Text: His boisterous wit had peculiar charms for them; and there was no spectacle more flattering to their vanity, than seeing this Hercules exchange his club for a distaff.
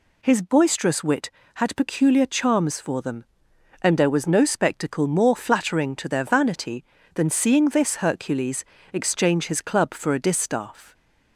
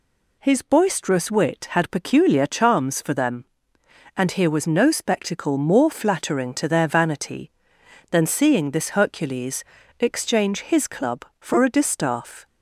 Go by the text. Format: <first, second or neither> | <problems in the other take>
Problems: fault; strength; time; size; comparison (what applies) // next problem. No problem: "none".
first | says "here" for "there"; at 4.2 s // pauses between "Hercules" and "exchange"; slight; at 9.6 s; 0.34 s long; slight in the first